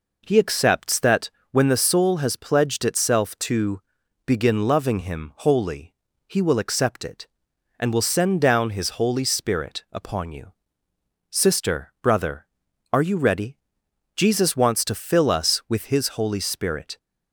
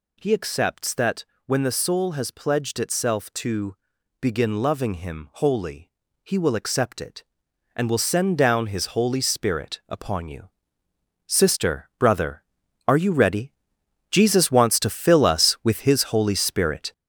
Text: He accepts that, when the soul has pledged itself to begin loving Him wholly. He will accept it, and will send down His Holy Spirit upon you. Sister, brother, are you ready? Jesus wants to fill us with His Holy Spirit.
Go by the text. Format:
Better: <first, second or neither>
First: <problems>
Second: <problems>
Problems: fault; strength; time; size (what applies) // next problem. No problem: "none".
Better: first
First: pauses between "to" and "begin"; noticeable; at 3.7 s; 0.46 s long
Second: gets louder; noticeable; throughout; 6 dB // pauses between "to" and "begin"; noticeable; at 3.7 s; 0.46 s long